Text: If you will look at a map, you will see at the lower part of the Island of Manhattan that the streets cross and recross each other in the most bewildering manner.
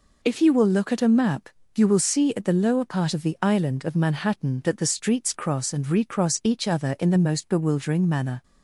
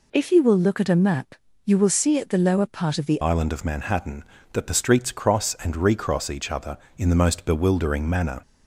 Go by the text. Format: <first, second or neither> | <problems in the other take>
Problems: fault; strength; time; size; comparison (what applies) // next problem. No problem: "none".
first | changes voice at "Island"; from 3.2 s on; 5.2 s long